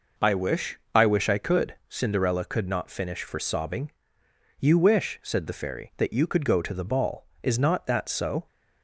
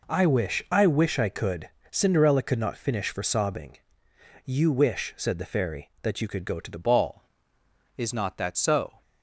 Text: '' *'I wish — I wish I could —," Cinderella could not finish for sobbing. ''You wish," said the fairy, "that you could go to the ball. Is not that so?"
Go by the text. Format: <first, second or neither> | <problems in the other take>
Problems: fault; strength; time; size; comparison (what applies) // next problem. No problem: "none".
first | changes voice at "ball"; from 6.8 s on; 2.2 s long